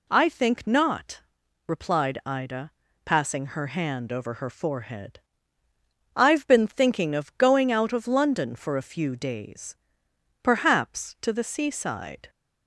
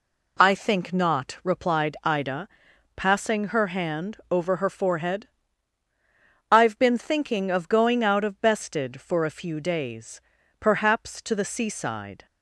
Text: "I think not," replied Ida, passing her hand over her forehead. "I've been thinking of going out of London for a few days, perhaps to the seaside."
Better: first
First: none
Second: says "Bested" for "London"; at 8.3 s

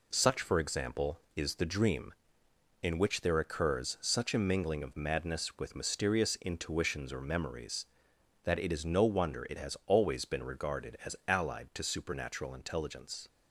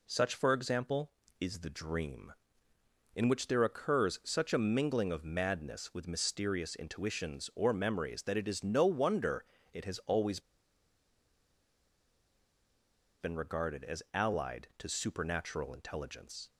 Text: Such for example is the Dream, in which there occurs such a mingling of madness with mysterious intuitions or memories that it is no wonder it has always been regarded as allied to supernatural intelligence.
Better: first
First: none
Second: pauses between "wonder" and "it"; slight; at 9.4 s; 0.28 s long // pauses between "always" and "been"; strong; at 10.3 s; 2.8 s long

